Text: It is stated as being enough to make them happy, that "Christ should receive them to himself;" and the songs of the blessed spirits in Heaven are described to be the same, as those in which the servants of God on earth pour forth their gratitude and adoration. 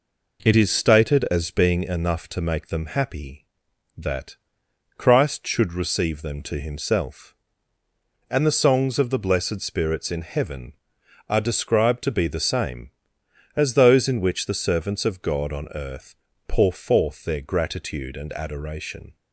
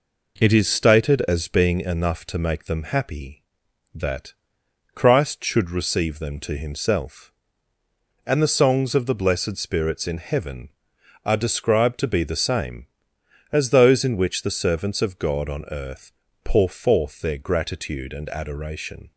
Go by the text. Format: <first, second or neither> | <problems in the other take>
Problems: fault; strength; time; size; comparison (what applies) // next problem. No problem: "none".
neither | pauses between "that" and "Christ"; noticeable; the same in both // pauses between "earth" and "pour"; slight; the same in both